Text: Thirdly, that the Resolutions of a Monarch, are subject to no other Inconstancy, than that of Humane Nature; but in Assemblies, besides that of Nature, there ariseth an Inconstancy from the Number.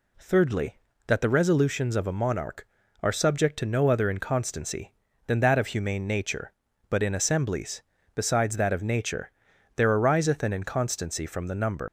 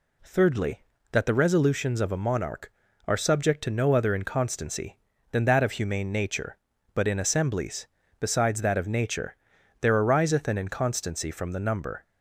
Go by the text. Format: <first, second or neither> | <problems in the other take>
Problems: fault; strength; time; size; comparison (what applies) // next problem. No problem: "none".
second | leaves "Number" unfinished; at 11.8 s; 105 ms